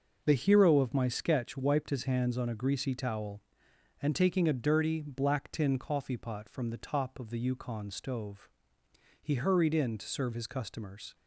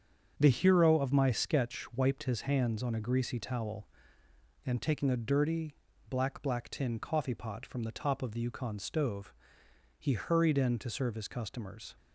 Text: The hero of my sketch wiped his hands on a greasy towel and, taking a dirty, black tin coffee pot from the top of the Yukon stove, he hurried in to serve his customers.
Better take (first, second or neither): first